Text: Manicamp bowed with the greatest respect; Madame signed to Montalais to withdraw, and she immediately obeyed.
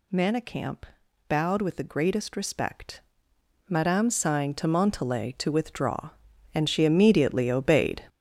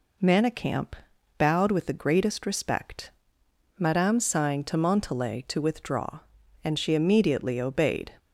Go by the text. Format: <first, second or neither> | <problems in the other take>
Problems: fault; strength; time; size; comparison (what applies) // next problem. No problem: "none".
second | gets louder; strong; throughout; 8.5 dB // pauses between "Manicamp" and "bowed"; at 0.8 s; 0.44 s long; also in the second